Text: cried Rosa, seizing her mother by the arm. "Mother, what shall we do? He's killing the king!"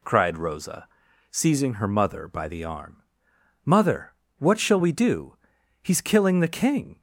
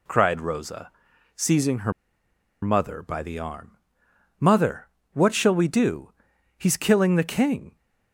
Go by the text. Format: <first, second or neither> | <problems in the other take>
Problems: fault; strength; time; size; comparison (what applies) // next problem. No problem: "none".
first | pauses between "her" and "mother"; noticeable; at 1.9 s; 0.70 s long